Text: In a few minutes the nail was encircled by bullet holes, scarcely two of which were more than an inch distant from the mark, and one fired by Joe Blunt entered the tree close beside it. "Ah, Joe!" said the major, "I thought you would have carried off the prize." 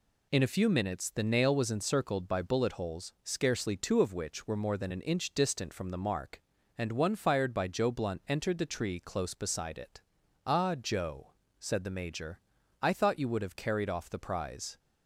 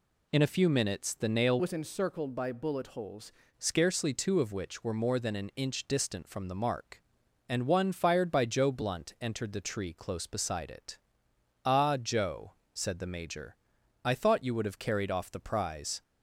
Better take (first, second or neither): first